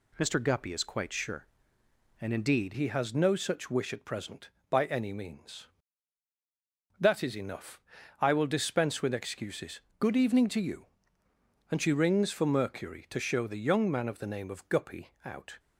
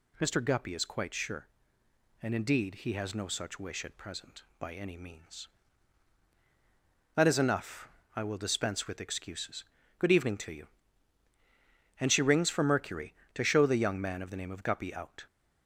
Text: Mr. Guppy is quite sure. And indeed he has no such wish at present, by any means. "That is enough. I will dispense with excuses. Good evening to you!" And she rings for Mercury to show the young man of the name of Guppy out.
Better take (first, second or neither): second